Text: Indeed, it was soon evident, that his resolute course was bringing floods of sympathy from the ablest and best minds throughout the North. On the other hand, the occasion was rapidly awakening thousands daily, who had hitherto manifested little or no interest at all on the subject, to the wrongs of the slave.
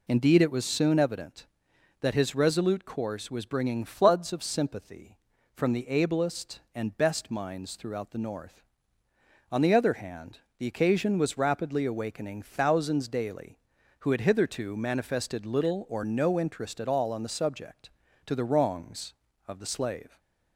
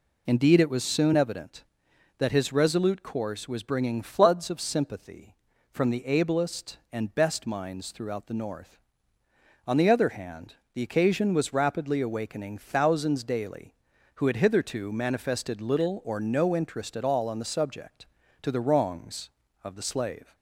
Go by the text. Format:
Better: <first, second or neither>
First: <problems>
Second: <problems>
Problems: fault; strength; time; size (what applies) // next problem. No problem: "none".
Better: neither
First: none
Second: none